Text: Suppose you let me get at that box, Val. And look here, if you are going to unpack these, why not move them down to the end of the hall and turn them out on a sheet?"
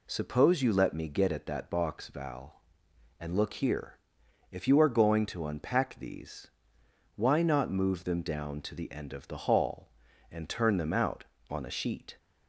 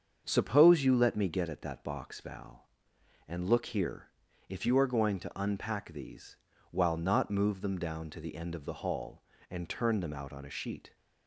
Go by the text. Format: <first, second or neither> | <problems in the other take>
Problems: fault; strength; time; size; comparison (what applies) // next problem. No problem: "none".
first | starts louder than the rest; strong; until 1.2 s; 7 dB // says "while" for "why"; at 6.7 s